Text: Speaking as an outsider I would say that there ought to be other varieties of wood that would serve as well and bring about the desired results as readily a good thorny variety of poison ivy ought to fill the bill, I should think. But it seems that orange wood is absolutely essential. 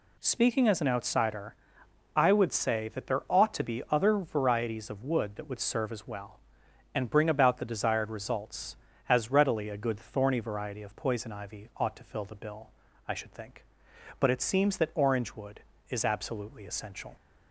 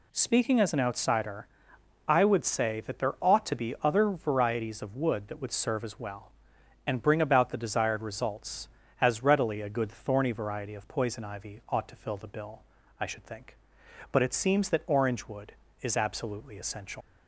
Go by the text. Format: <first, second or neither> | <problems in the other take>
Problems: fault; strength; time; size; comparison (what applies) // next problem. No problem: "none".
first | pauses between "outsider" and "I"; noticeable; at 1.4 s; 0.62 s long; noticeable in the first // leaves "essential" unfinished; at 17.0 s; 65 ms